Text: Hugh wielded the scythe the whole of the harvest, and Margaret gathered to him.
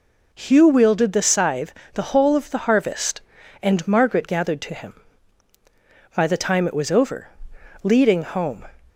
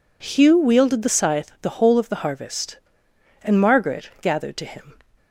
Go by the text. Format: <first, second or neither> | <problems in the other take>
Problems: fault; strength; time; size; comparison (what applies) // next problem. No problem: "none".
second | pauses between "scythe" and "the"; slight; at 1.7 s; 0.18 s long // goes on to say "By the time it was over leading home"; strong; from 6.1 s on; 2.4 s long